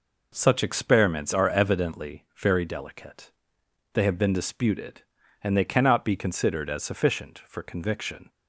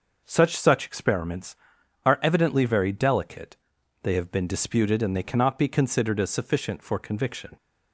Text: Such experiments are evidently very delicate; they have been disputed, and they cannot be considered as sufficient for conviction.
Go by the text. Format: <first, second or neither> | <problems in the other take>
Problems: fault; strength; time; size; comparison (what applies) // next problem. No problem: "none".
first | says "Such" twice; at 0.5 s